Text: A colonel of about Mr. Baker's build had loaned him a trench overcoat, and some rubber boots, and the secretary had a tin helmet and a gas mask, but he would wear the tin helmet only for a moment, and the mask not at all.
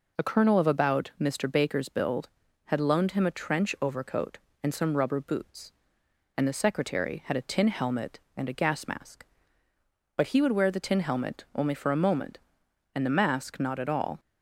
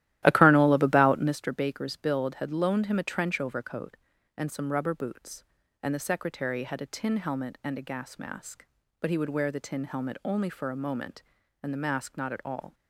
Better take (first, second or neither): first